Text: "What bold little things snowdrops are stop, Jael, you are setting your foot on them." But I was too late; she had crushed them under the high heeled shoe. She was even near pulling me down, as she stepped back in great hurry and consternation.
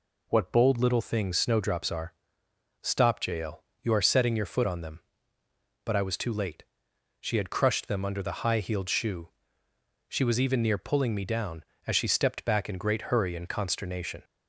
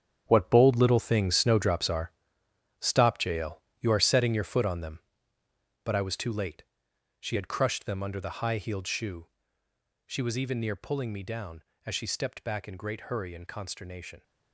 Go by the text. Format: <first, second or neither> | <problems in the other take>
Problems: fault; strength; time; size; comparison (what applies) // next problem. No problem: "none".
first | gets quieter; strong; throughout; 12 dB // pauses between "are" and "stop"; noticeable; at 2.1 s; 0.70 s long; noticeable in the first